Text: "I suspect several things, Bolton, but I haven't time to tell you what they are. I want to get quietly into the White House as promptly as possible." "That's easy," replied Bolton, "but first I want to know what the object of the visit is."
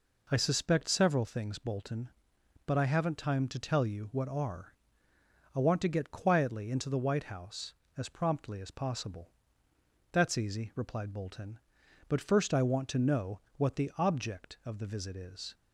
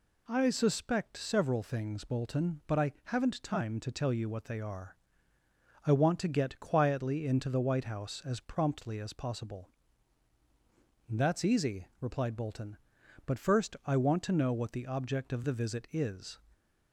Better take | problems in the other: second | skips "they"; at 4.2 s // pauses between "know" and "what"; slight; at 13.3 s; 0.18 s long

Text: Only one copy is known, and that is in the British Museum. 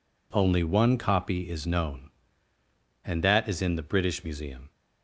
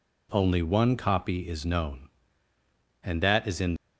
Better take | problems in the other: first | stops before "the British Museum"; at 3.7 s

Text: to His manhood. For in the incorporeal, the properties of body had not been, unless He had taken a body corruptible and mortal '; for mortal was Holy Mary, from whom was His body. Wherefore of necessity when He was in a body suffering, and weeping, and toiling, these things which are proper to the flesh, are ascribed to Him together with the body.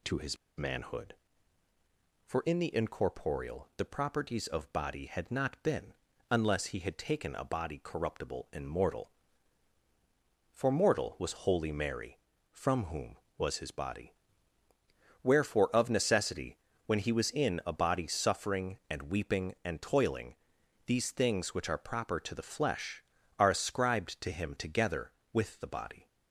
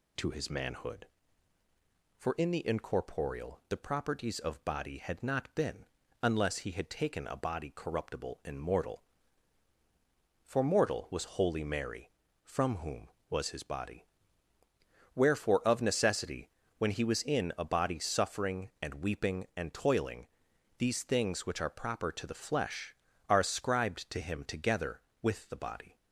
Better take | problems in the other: second | pauses between "His" and "manhood"; slight; at 0.3 s; 0.21 s long // pauses between "necessity" and "when"; slight; at 16.5 s; 0.28 s long; slight in the second

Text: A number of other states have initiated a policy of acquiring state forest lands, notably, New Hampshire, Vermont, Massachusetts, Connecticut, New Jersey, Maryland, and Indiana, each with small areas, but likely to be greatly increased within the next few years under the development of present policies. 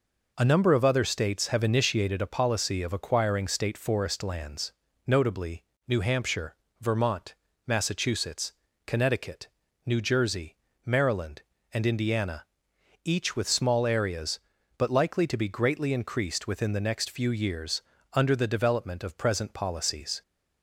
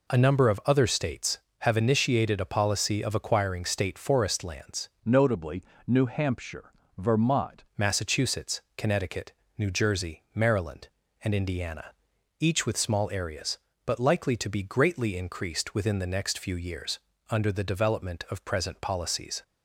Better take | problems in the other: first | changes voice from "notably" to "Vermont"; from 5.0 to 7.6 s; 2.6 s long // pauses between "years" and "under"; slight; at 16.9 s; 0.30 s long; slight in the first

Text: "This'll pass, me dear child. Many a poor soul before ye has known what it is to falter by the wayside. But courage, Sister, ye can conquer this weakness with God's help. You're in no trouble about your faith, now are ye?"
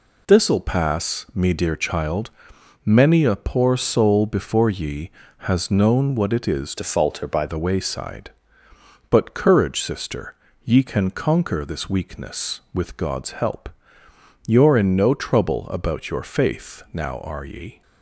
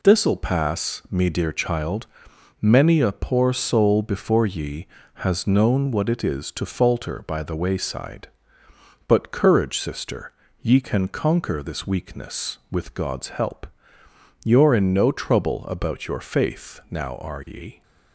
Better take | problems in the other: second | changes voice from "to" to "by"; from 6.7 to 7.4 s; 0.7 s long

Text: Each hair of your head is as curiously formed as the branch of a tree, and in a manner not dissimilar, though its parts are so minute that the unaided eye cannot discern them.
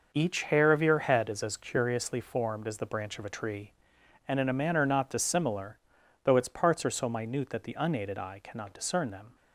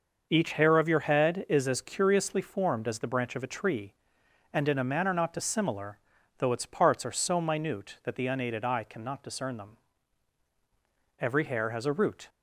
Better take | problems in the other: first | starts louder than the rest; noticeable; until 1.3 s; 6 dB // goes on to say "Every hair has a root"; noticeable; from 11.2 s on; 1.0 s long

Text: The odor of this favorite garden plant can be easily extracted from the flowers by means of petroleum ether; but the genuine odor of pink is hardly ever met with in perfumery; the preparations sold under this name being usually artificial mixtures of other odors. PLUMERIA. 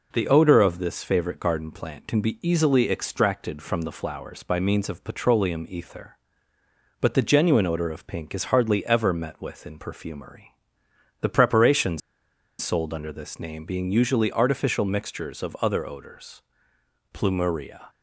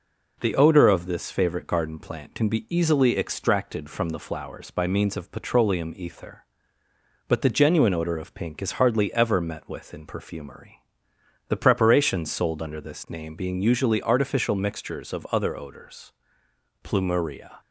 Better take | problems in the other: second | pauses between "preparations" and "sold"; noticeable; at 12.0 s; 0.61 s long

